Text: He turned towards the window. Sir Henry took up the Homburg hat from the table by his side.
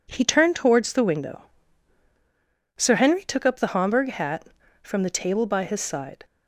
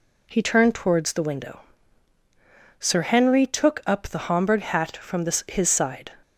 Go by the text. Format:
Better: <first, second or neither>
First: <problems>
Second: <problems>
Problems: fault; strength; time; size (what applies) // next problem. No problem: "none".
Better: first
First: none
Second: skips "table by"; at 5.4 s